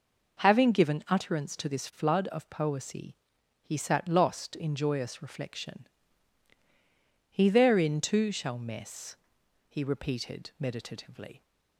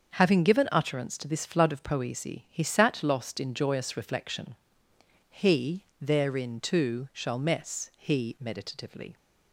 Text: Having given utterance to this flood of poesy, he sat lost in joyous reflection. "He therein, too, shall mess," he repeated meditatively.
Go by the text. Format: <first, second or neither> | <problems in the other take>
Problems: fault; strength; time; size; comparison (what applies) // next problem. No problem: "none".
first | starts louder than the rest; until 1.1 s; 7 dB // pauses between "He" and "therein"; slight; at 5.8 s; 0.16 s long // skips "repeated"; at 8.3 s